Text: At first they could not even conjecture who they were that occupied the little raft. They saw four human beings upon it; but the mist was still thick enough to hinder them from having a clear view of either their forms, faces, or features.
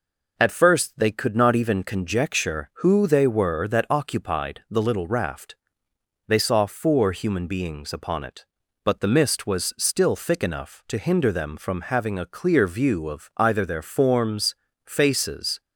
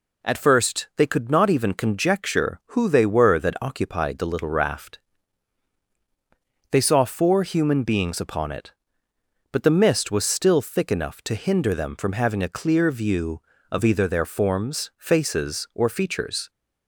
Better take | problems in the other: second | stops before "or features"; at 15.6 s

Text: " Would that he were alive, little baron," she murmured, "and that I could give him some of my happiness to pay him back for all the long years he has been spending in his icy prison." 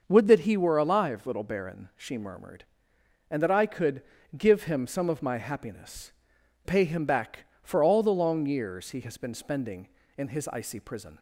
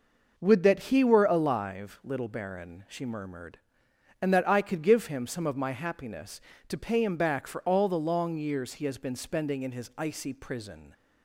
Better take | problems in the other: second | starts louder than the rest; noticeable; until 1.0 s; 6 dB // pauses between "could" and "give"; slight; at 4.0 s; 0.34 s long // skips "to"; at 6.3 s

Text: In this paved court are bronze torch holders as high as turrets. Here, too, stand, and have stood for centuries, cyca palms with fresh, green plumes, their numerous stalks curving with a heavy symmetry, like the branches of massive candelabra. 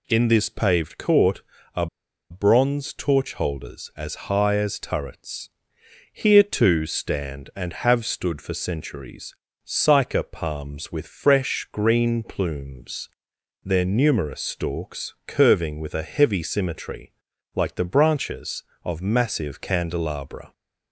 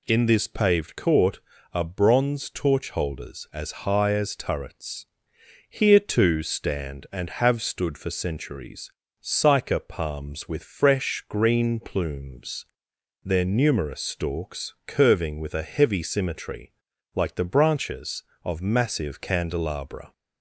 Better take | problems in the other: second | pauses between "are" and "bronze"; at 1.8 s; 0.43 s long

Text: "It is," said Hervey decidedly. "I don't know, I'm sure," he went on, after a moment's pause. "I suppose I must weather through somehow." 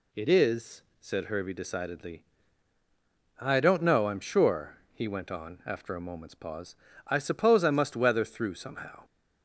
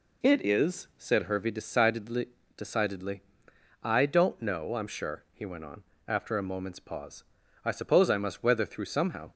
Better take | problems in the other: first | says "decidedly" twice; at 2.5 s

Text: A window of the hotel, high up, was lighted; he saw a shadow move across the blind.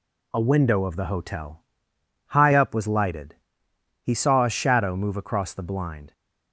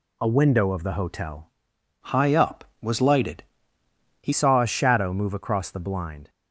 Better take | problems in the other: first | changes voice from "high" to "he"; from 2.0 to 4.3 s; 2.3 s long

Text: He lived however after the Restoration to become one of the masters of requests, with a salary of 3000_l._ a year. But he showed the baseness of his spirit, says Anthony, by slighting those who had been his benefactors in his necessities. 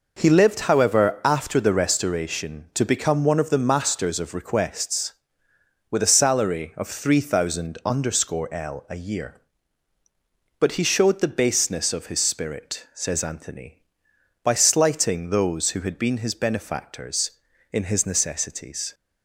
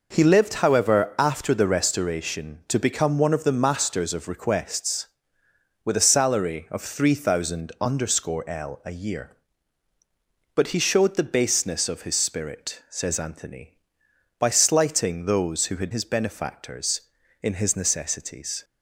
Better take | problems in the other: first | skips "been"; at 15.9 s

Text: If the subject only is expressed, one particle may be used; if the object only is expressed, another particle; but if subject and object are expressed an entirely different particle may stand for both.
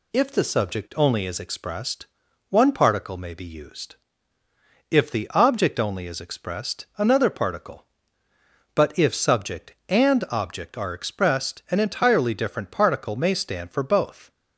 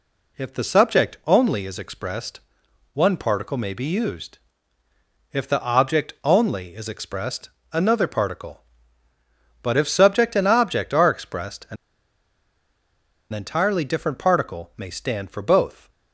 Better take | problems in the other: first | pauses between "an" and "entirely"; strong; at 11.7 s; 1.5 s long

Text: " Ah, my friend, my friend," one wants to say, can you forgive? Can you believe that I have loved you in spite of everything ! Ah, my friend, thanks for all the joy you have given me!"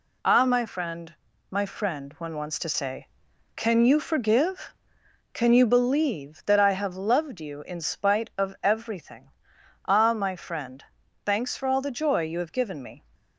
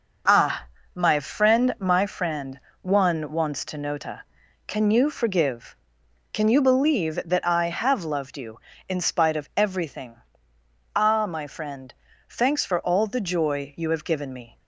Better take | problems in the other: first | says "nota" for "say"; at 3.7 s

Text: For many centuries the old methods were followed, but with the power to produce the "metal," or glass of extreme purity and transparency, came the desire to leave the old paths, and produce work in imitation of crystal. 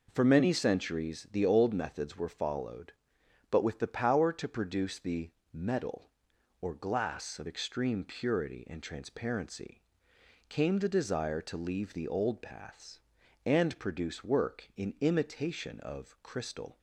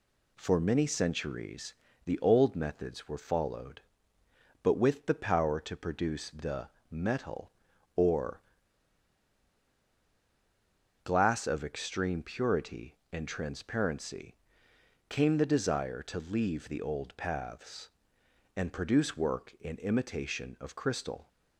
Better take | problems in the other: first | pauses between "centuries" and "the"; slight; at 1.7 s; 0.30 s long // pauses between "the" and "metal"; slight; at 6.6 s; 0.24 s long; slight in the first // pauses between "or" and "glass"; strong; at 8.4 s; 2.6 s long

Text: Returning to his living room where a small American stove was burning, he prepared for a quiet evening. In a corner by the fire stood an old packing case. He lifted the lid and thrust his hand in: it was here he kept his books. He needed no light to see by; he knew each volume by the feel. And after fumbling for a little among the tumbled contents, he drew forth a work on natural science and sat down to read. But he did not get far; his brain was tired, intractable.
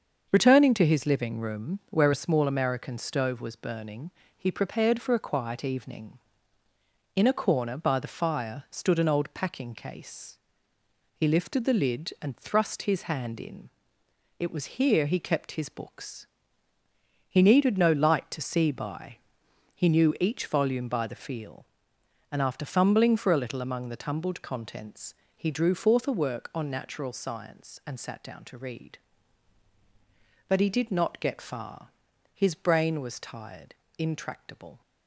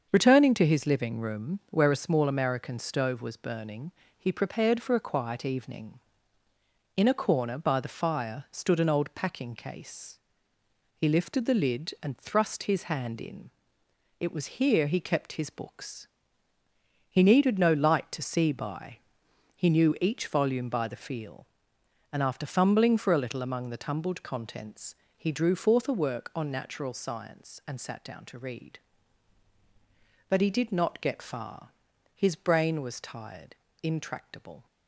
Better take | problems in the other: neither | starts louder than the rest; the same in both

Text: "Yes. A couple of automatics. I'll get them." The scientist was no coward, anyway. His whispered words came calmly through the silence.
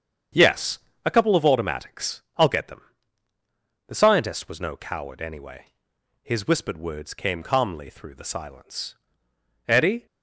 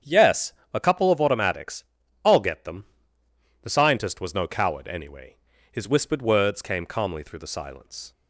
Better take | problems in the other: second | starts louder than the rest; strong; until 1.6 s; 7.5 dB; strong in the second // goes on to say "Eddie"; slight; from 9.6 s on; 0.38 s long

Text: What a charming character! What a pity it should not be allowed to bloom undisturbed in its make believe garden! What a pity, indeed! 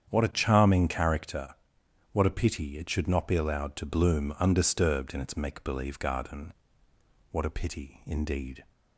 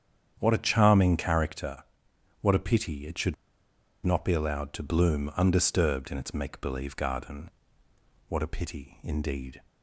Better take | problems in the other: first | starts louder than the rest; strong; until 1.4 s; 8.5 dB; strong in the first // pauses between "should" and "not"; noticeable; at 3.3 s; 0.69 s long

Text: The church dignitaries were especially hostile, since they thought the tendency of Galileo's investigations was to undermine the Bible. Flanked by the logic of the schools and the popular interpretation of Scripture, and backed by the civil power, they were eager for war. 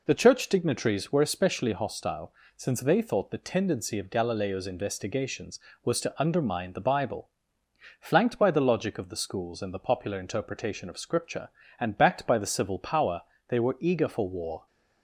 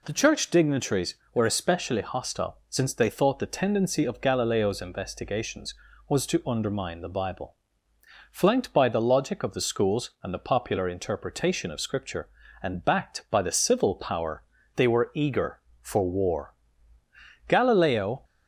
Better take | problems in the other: first | goes on to say "Galileo"; noticeable; from 17.4 s on; 0.76 s long

